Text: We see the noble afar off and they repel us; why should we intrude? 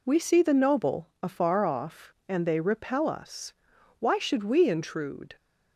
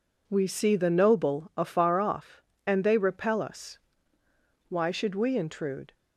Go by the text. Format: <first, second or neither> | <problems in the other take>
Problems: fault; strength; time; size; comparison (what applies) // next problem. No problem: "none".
neither | none